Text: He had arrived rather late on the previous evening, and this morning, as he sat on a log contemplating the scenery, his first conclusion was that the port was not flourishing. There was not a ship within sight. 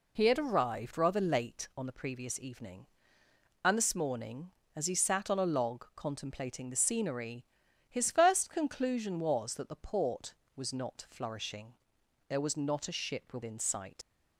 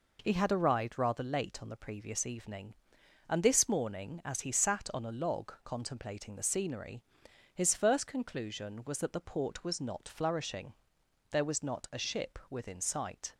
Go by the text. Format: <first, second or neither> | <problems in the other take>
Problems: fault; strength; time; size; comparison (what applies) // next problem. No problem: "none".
second | leaves "sight" unfinished; at 14.0 s; 70 ms